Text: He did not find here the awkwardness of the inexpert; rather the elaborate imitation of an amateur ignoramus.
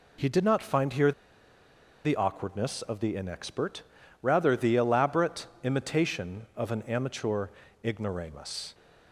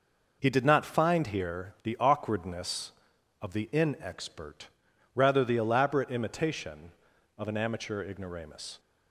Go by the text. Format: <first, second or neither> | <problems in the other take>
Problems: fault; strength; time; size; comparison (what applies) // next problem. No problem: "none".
second | pauses between "here" and "the"; noticeable; at 1.1 s; 0.91 s long // pauses between "elaborate" and "imitation"; slight; at 5.4 s; 0.16 s long // pauses between "amateur" and "ignoramus"; slight; at 7.4 s; 0.36 s long